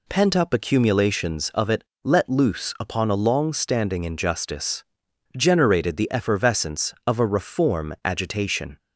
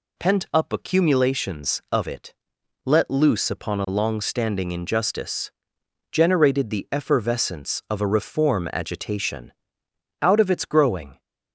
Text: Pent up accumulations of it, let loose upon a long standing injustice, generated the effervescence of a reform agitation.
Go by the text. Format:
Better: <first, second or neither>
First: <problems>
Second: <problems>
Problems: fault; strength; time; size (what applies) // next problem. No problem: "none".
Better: first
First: none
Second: goes on to say "Out of its growing"; noticeable; from 10.2 s on; 0.98 s long